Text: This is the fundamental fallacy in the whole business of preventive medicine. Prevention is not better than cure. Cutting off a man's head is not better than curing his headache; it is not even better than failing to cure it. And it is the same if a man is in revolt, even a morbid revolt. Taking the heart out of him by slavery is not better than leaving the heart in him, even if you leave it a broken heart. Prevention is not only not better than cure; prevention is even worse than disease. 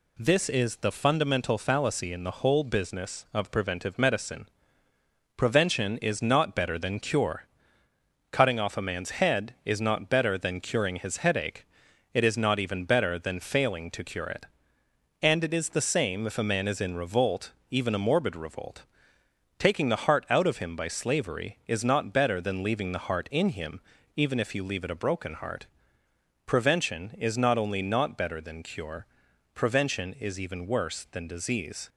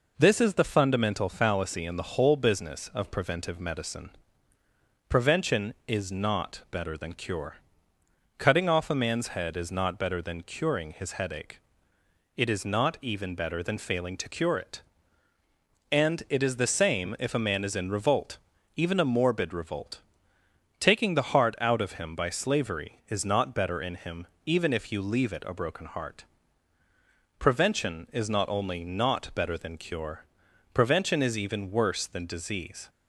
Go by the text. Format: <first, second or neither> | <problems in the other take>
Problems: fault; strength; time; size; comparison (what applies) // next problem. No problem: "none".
first | skips "than leaving the heart"; at 23.8 s